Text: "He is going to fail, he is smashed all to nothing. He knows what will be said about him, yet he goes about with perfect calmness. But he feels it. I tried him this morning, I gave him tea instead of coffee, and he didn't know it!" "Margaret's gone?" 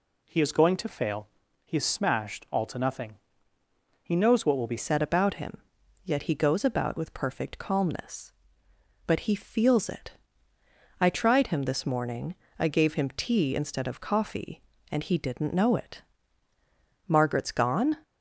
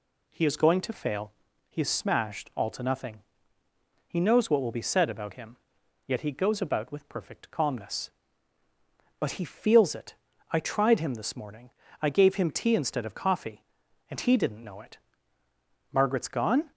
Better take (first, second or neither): second